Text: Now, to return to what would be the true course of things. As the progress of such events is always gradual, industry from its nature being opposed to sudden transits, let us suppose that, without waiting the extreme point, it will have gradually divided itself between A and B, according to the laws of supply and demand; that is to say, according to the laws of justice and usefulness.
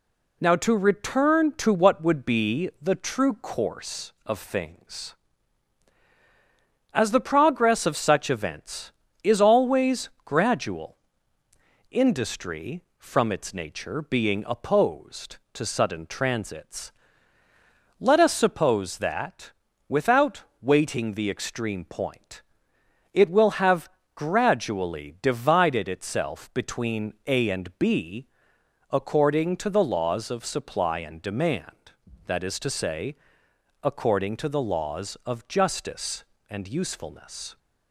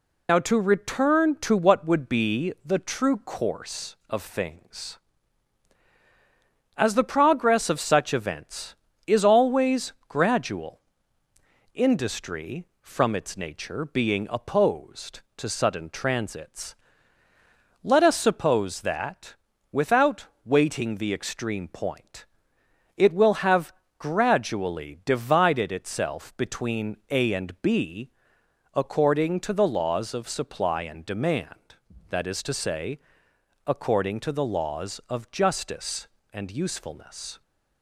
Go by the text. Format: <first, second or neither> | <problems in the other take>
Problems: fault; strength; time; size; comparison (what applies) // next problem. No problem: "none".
first | loses the start of "Now"; at 0.2 s; 55 ms // pauses between "without" and "waiting"; slight; at 20.2 s; 0.18 s long; slight in the first // pauses between "have" and "gradually"; slight; at 23.7 s; 0.26 s long; slight in the first